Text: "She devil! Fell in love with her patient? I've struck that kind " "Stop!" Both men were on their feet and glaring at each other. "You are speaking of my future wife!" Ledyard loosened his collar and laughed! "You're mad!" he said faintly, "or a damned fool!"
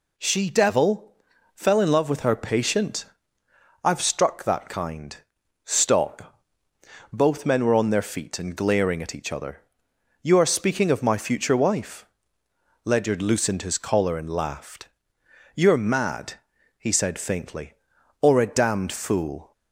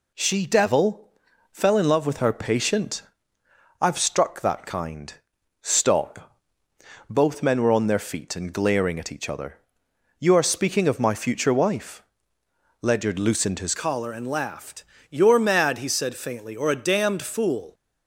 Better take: first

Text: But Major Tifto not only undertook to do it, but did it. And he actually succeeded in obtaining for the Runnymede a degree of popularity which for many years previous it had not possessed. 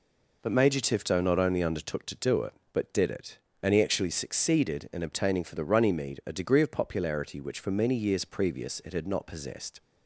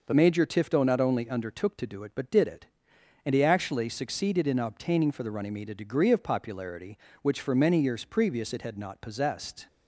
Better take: first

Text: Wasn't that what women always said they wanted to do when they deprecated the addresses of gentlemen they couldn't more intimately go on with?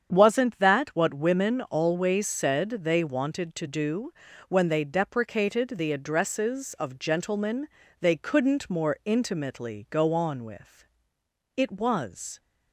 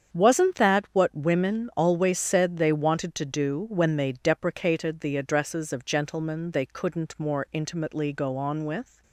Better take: second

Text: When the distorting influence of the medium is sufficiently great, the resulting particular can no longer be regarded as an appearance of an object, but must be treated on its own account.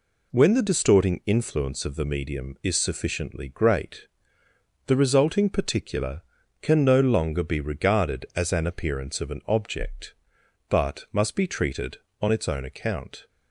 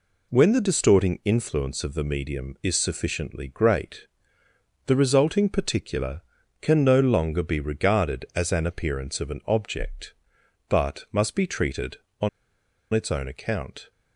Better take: first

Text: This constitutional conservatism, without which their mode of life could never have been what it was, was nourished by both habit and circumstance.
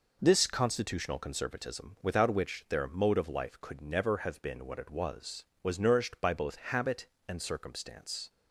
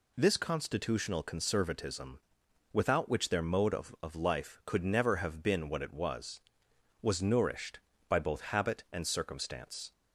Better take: first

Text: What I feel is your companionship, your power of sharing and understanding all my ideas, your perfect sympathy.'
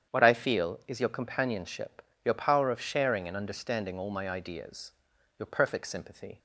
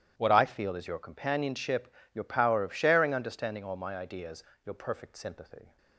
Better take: first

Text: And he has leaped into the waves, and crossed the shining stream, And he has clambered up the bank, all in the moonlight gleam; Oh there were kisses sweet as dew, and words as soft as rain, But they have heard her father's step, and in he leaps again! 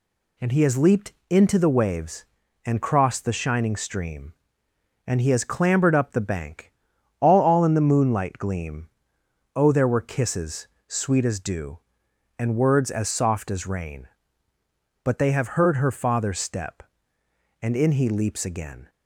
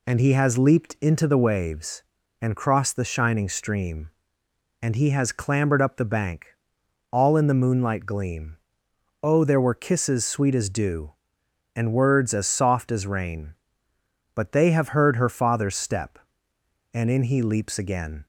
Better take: second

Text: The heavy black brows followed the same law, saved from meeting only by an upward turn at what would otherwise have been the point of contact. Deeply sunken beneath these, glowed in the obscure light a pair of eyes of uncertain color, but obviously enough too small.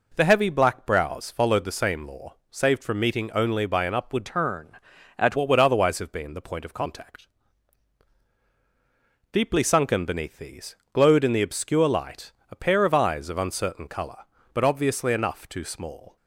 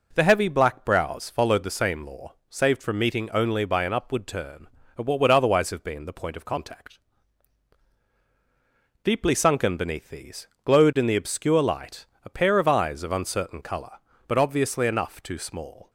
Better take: second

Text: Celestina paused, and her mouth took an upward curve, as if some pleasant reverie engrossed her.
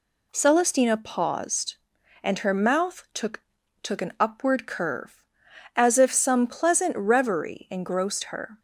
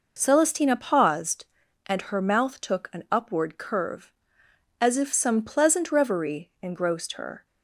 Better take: second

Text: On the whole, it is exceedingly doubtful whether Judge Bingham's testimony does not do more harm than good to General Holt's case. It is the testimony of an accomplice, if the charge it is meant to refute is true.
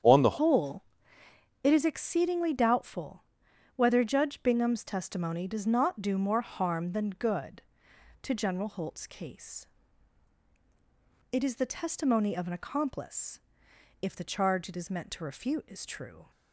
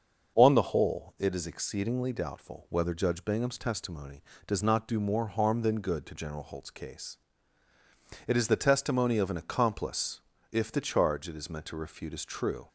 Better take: second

